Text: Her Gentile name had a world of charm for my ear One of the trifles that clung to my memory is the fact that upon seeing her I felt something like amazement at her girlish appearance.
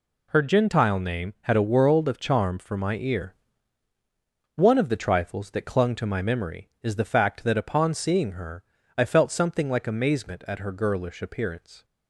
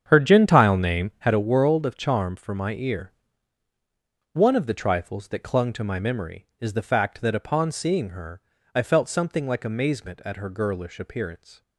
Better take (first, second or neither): first